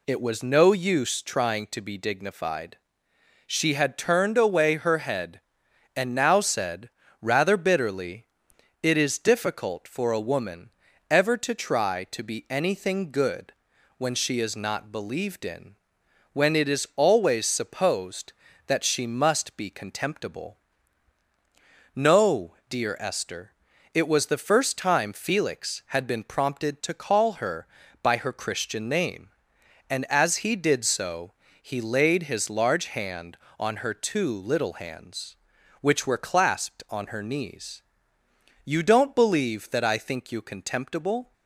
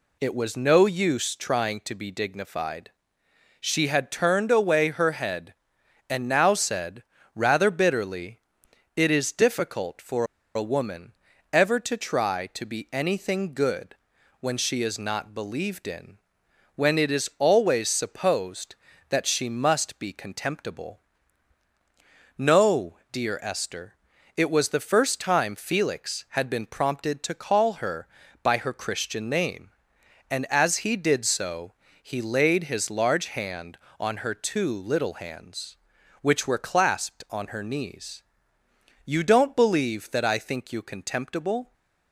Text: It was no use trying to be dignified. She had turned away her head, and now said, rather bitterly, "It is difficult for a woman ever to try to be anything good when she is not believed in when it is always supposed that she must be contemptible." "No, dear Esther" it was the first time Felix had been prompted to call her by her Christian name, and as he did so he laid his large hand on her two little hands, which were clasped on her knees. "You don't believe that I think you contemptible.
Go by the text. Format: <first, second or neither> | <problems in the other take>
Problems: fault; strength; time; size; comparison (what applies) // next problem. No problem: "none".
first | pauses between "for" and "a"; slight; at 10.2 s; 0.31 s long // pauses between "woman" and "ever"; at 11.1 s; 0.38 s long; also in the first // pauses between "good" and "when"; at 13.9 s; 0.44 s long; also in the first // pauses between "in" and "when"; noticeable; at 16.1 s; 0.58 s long; noticeable in the first // pauses between "Esther" and "it"; at 23.9 s; 0.42 s long; also in the first // pauses between "so" and "he"; slight; at 31.7 s; 0.30 s long; slight in the first